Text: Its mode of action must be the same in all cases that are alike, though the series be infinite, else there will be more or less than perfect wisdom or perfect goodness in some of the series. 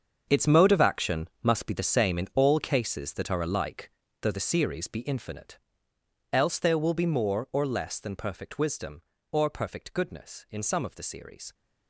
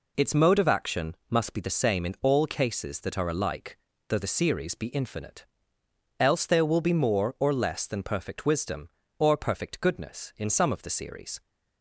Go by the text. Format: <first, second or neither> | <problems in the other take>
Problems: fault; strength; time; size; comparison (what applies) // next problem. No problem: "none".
second | gets quieter; strong; throughout; 13 dB // pauses between "action" and "must"; slight; at 1.2 s; 0.16 s long; slight in the second